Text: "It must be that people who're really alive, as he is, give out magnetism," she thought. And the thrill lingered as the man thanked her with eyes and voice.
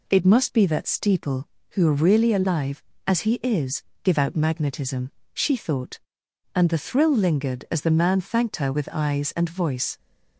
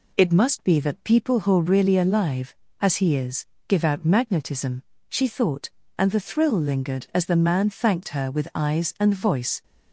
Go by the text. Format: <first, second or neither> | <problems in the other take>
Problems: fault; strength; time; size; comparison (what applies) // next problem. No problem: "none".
second | says "steeple" for "people"; at 0.8 s